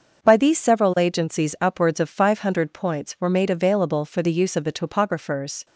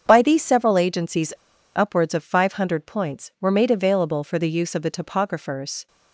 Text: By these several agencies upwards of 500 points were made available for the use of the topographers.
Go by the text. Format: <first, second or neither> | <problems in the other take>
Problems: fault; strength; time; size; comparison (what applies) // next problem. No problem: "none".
first | starts louder than the rest; strong; until 1.0 s; 7.5 dB; also in the first // pauses between "agencies" and "upwards"; at 1.3 s; 0.42 s long